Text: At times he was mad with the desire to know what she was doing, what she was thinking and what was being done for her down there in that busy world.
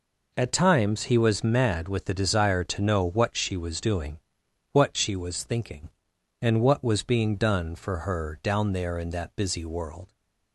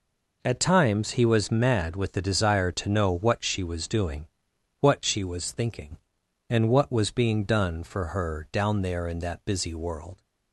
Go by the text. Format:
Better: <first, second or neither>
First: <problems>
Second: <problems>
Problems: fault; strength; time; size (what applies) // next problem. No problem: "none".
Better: neither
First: none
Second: none